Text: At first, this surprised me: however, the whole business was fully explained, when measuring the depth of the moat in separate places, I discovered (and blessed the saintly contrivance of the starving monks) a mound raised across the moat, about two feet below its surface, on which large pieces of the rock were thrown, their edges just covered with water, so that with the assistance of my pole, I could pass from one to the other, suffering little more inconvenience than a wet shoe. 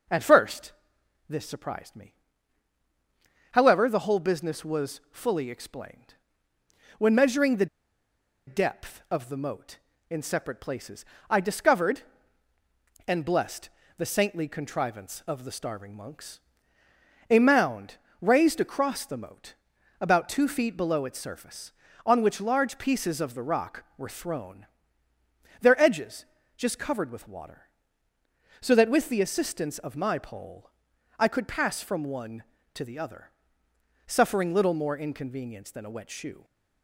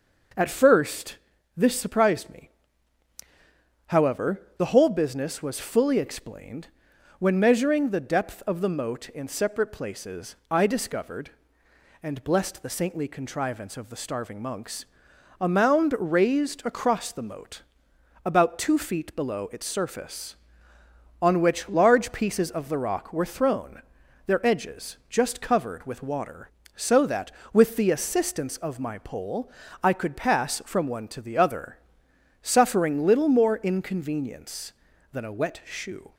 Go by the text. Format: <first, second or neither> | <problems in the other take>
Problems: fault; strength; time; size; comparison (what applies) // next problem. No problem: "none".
second | pauses between "the" and "depth"; noticeable; at 7.6 s; 0.81 s long // pauses between "blessed" and "the"; slight; at 13.6 s; 0.28 s long // pauses between "mound" and "raised"; slight; at 17.9 s; 0.24 s long // pauses between "edges" and "just"; slight; at 26.2 s; 0.32 s long